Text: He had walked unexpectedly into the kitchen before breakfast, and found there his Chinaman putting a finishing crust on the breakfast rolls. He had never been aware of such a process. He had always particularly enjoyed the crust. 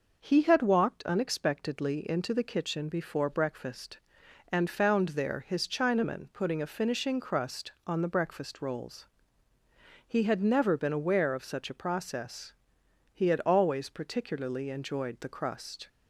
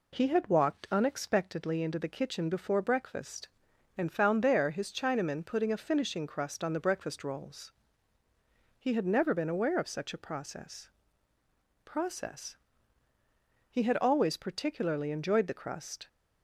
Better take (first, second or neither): first